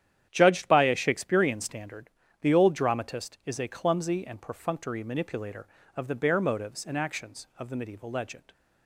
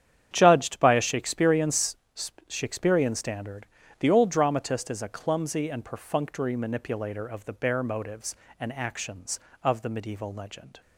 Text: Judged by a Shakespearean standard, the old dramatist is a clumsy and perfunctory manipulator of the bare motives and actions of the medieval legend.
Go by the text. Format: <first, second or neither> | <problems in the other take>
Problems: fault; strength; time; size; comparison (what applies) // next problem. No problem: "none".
first | starts louder than the rest; strong; until 1.3 s; 10.5 dB; strong in the first // says "Shakespearean" twice; at 2.4 s